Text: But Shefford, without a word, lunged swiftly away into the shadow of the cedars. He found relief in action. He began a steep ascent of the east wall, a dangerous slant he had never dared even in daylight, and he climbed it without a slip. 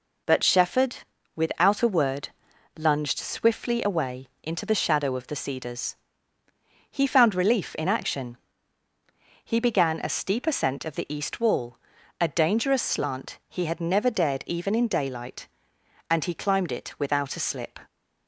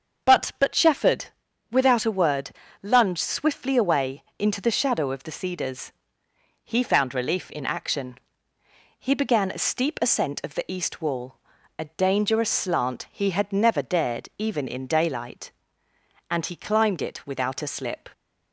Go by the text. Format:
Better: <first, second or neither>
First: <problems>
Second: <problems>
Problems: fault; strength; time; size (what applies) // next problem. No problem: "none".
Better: first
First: none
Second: starts louder than the rest; until 1.7 s; 7 dB // says "But" twice; at 0.5 s // pauses between "away" and "into"; slight; at 4.2 s; 0.16 s long